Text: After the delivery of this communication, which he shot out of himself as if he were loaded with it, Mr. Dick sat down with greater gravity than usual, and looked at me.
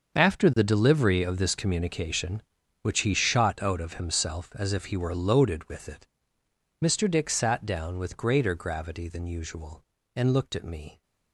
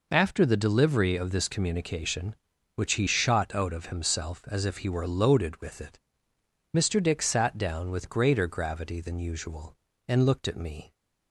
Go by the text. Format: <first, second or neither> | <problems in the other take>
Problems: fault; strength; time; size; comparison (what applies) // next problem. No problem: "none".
second | gets quieter; strong; throughout; 14 dB